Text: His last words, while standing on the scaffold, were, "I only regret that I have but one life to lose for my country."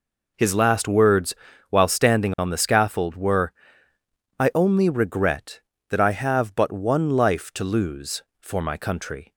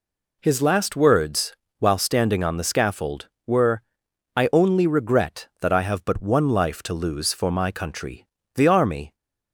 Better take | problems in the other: first | goes on to say "The army"; from 8.5 s on; 0.60 s long

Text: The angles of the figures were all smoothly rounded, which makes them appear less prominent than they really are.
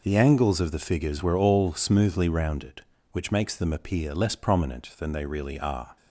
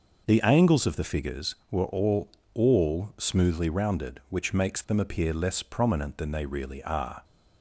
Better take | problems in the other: first | says "all" twice; at 2.5 s

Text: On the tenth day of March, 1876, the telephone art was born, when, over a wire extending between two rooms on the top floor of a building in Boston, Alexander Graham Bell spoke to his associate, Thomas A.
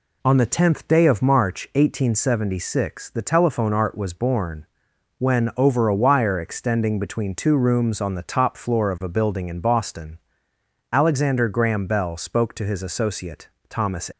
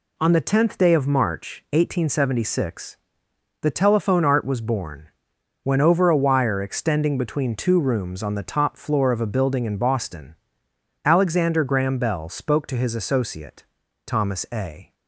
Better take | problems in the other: second | stops before "A"; at 14.1 s

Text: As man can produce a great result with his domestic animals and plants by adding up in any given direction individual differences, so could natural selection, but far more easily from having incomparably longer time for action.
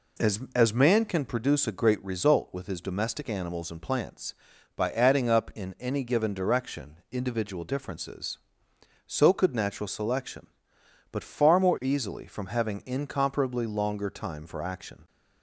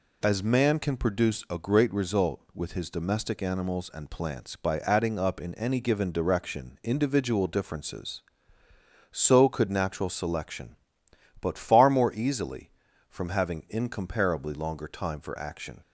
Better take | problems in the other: second | says "As" twice; at 0.5 s

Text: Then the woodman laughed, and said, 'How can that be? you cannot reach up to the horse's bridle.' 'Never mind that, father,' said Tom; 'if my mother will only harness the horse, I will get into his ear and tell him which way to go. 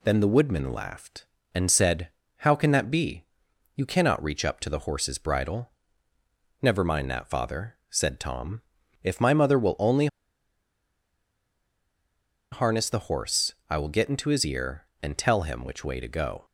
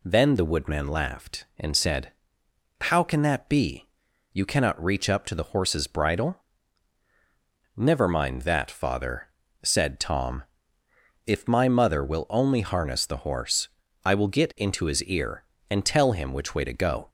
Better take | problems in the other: second | pauses between "only" and "harness"; strong; at 10.0 s; 2.4 s long

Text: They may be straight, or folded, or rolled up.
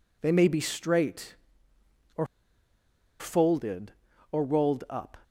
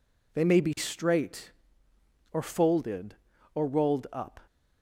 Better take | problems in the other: second | pauses between "or" and "folded"; noticeable; at 2.2 s; 0.93 s long

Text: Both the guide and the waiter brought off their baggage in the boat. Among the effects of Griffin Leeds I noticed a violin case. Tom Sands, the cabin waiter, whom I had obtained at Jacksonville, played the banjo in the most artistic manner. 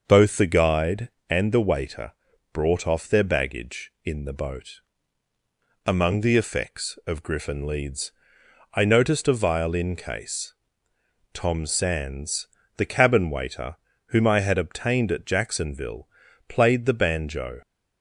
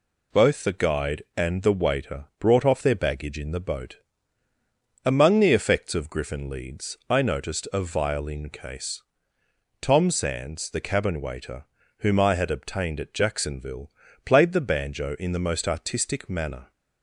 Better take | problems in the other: second | starts louder than the rest; until 1.0 s; 6 dB // pauses between "waiter" and "brought"; at 2.1 s; 0.42 s long // pauses between "Leeds" and "I"; noticeable; at 8.1 s; 0.64 s long // stops before "in the most artistic manner"; at 17.6 s

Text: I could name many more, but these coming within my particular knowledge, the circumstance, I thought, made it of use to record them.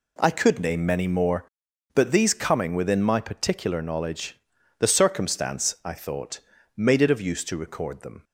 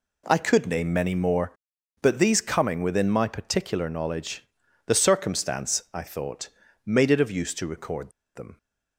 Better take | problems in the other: first | pauses between "record" and "them"; slight; at 8.1 s; 0.23 s long

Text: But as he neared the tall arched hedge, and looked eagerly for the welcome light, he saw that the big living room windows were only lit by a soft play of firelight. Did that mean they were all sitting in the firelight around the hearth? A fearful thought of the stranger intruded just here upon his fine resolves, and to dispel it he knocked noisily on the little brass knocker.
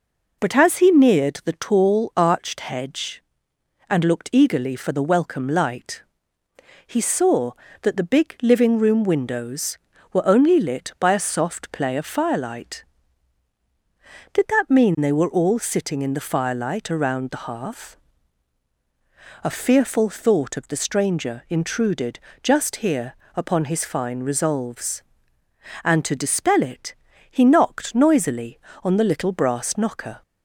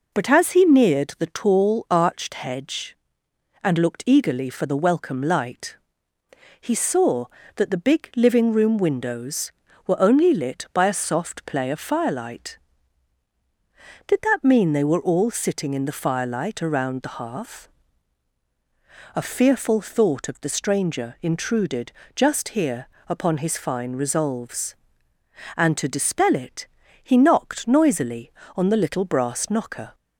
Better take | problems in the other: neither | pauses between "intruded" and "just"; slight; the same in both // pauses between "here" and "upon"; slight; the same in both // pauses between "it" and "he"; slight; the same in both

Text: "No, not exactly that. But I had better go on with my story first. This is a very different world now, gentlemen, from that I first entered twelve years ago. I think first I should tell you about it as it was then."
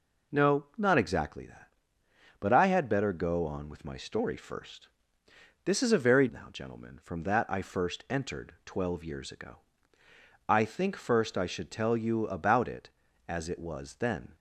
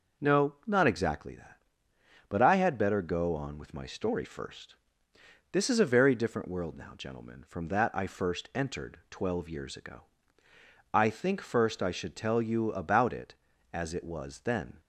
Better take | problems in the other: second | skips "different world"; at 6.2 s

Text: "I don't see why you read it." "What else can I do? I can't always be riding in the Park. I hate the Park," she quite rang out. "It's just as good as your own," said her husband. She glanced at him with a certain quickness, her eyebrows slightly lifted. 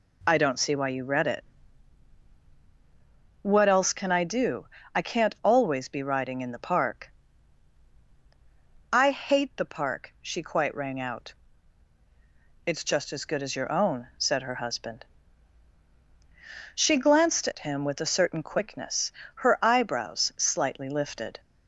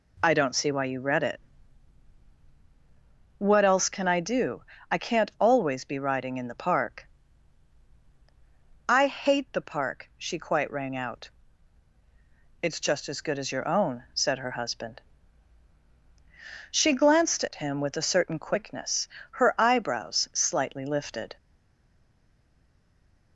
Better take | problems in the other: first | stays silent after the last word; noticeable; from 21.3 s on; 2.0 s long

